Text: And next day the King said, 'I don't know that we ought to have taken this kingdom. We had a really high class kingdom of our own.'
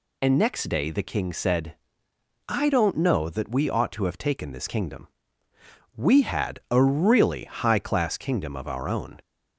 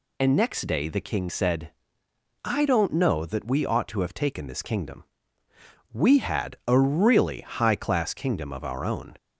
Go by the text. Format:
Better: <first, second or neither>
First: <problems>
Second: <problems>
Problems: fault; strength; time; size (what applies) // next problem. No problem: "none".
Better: neither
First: none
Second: none